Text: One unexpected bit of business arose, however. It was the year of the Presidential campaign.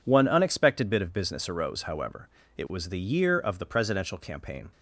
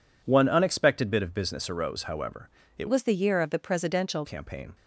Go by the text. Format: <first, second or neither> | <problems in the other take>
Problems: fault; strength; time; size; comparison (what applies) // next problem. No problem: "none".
first | changes voice from "was" to "Presidential"; from 2.8 to 4.2 s; 1.4 s long